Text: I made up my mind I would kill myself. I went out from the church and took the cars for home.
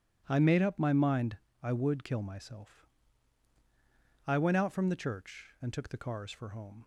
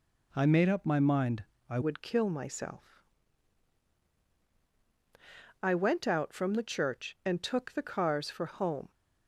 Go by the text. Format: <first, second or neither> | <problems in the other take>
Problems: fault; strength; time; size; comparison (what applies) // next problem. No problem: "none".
first | pauses between "mind" and "I"; slight; at 1.4 s; 0.26 s long; slight in the first // changes voice at "would"; from 1.8 s on; 7.1 s long